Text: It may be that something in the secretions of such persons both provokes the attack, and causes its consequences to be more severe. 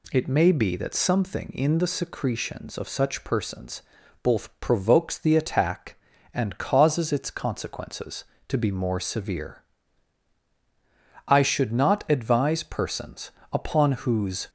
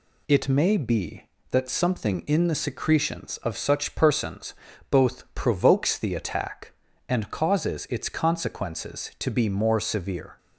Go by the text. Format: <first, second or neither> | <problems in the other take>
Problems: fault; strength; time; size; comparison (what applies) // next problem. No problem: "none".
second | pauses between "persons" and "both"; at 3.8 s; 0.42 s long; slight in the second // goes on to say "I should not advise persons upon whose"; strong; from 11.2 s on; 3.2 s long